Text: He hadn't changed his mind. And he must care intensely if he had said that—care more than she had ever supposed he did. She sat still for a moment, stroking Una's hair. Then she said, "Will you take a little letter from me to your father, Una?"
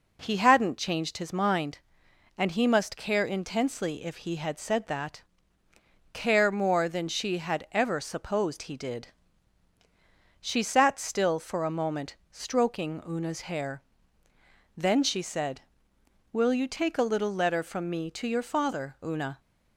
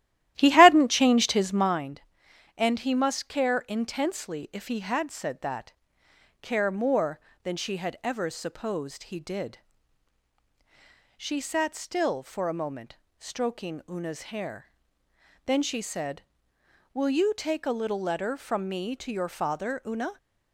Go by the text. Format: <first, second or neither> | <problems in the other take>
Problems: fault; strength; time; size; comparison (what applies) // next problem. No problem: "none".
first | starts louder than the rest; strong; until 1.9 s; 13.5 dB